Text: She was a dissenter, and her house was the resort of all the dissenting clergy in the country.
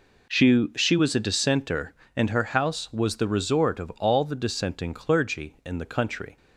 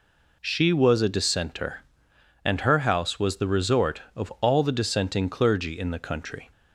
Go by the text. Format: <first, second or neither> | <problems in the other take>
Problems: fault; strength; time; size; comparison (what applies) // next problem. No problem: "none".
second | says "She" twice; at 0.7 s